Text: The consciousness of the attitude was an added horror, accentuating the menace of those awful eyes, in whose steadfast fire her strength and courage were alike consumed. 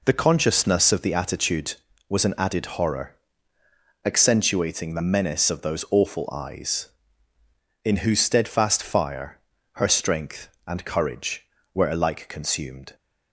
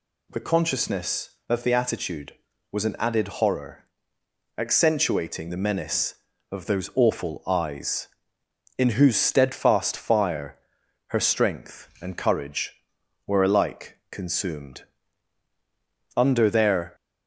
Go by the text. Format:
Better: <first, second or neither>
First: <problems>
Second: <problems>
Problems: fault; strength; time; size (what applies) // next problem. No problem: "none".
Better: first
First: pauses between "fire" and "her"; slight; at 9.3 s; 0.36 s long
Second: pauses between "fire" and "her"; noticeable; at 10.5 s; 0.52 s long // goes on to say "Under their"; noticeable; from 16.1 s on; 0.78 s long